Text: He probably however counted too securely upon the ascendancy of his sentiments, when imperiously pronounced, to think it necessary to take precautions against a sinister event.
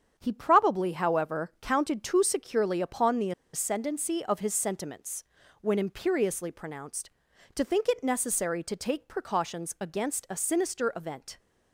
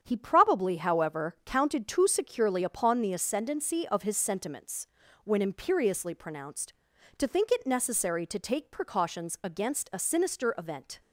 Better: second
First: starts louder than the rest; strong; until 1.1 s; 8 dB // pauses between "the" and "ascendancy"; slight; at 3.3 s; 0.22 s long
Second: starts louder than the rest; strong; until 1.0 s; 8 dB

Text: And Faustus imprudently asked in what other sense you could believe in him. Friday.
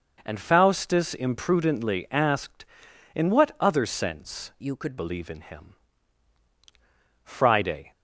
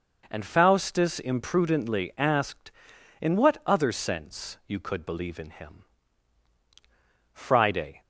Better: second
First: changes voice from "you" to "could"; from 4.6 to 4.9 s; 0.3 s long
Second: none

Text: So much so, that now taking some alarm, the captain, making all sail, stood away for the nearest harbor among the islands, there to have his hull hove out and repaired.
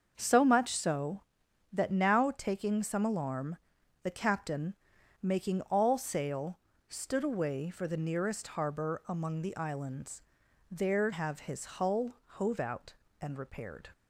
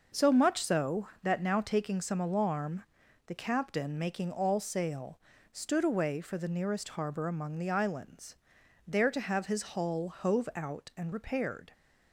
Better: second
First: starts louder than the rest; until 1.1 s; 6.5 dB // skips "to"; at 11.1 s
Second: none

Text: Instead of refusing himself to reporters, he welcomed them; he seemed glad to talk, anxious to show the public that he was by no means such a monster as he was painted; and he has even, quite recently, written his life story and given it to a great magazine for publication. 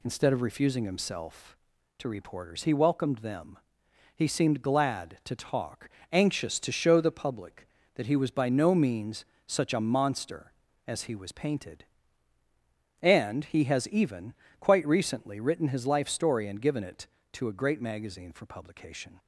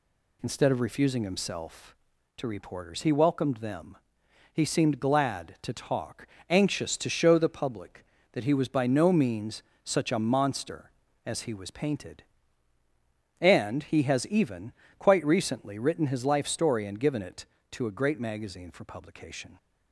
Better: neither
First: pauses between "means" and "such"; slight; at 9.2 s; 0.22 s long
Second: pauses between "means" and "such"; slight; at 9.6 s; 0.22 s long

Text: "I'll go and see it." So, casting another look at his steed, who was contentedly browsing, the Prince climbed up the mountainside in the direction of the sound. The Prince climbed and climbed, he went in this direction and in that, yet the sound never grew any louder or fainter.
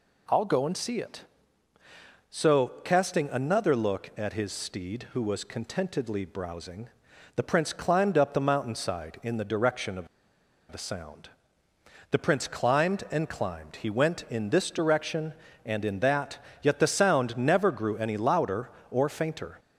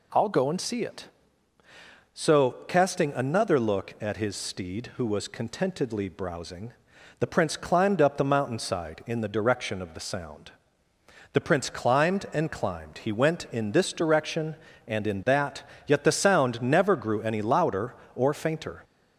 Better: second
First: pauses between "of" and "the"; noticeable; at 10.0 s; 0.63 s long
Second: none

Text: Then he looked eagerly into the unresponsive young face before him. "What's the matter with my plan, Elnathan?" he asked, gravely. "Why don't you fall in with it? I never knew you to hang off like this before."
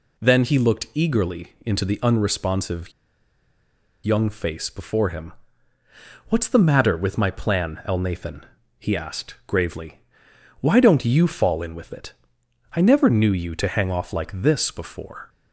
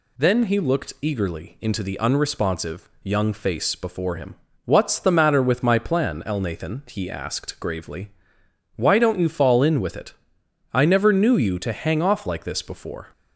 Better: second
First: pauses between "unresponsive" and "young"; at 2.9 s; 1.1 s long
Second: none

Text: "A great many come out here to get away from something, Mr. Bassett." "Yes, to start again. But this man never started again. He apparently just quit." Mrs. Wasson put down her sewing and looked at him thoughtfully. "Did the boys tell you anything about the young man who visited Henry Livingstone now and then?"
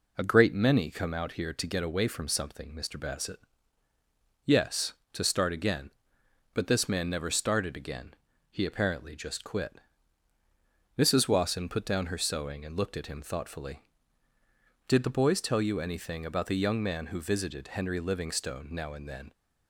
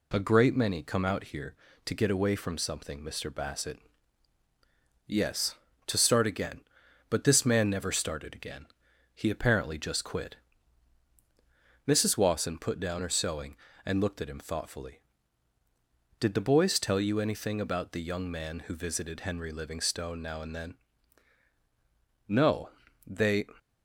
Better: first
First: none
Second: goes on to say "No They"; noticeable; from 22.2 s on; 1.1 s long

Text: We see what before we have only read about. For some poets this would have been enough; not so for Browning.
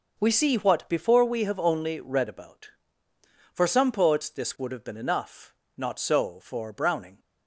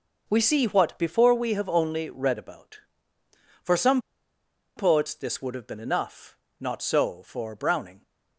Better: first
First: none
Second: pauses between "some" and "poets"; noticeable; at 4.0 s; 0.76 s long

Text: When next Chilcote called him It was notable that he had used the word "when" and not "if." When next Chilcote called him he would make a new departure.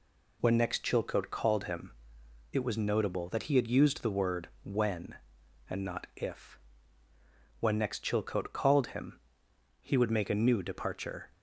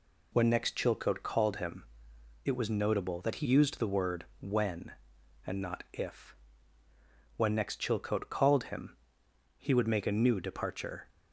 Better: first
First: pauses between "him" and "It"; noticeable; at 1.9 s; 0.60 s long // pauses between "him" and "he"; noticeable; at 9.1 s; 0.62 s long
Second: pauses between "him" and "It"; noticeable; at 1.8 s; 0.60 s long // skips "had"; at 3.4 s // pauses between "him" and "he"; noticeable; at 8.9 s; 0.62 s long

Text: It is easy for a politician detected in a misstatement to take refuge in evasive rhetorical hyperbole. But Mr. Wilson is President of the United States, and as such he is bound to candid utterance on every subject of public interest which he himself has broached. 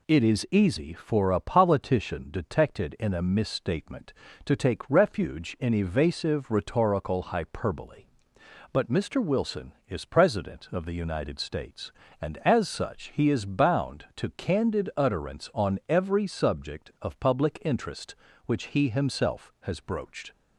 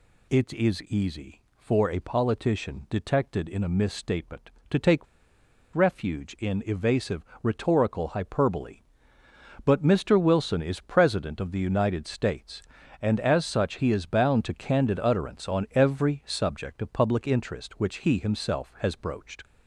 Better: first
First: none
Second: pauses between "take" and "refuge"; noticeable; at 5.0 s; 0.69 s long // pauses between "evasive" and "rhetorical"; slight; at 7.2 s; 0.18 s long

